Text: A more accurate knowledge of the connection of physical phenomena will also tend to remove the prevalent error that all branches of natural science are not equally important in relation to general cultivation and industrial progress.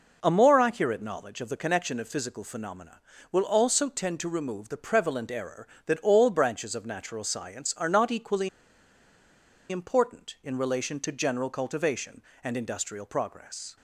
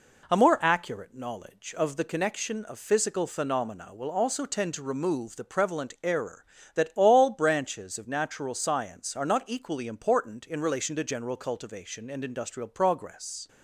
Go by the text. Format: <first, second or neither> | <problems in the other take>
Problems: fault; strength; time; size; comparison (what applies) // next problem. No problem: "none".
second | pauses between "equally" and "important"; at 8.4 s; 1.2 s long